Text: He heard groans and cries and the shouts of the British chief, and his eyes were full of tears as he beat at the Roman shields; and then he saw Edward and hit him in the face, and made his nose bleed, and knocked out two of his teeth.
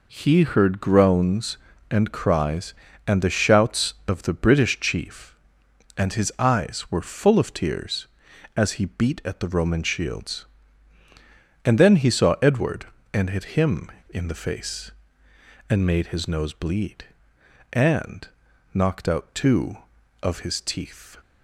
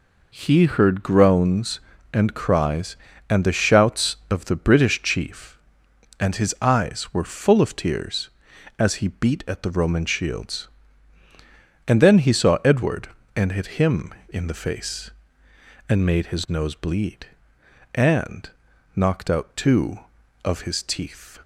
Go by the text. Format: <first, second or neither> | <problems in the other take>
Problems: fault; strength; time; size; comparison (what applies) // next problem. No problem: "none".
neither | pauses between "and" and "knocked"; noticeable; the same in both